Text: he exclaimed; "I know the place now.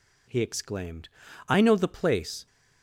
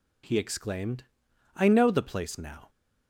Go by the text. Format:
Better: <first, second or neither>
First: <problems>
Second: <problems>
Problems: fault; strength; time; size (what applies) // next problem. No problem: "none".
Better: second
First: stops before "now"; at 2.4 s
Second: none